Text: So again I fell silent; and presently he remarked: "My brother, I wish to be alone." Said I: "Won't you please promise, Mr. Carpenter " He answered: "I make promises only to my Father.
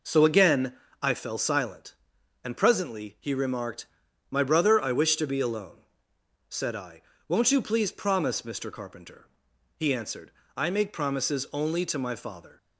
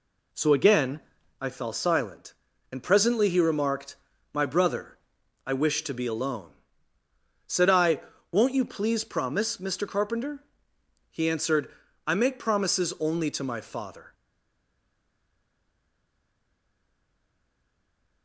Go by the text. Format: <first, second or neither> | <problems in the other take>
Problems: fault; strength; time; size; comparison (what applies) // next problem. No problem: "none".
first | pauses between "again" and "I"; at 0.9 s; 0.40 s long; slight in the first // stays silent after the last word; strong; from 14.1 s on; 4.1 s long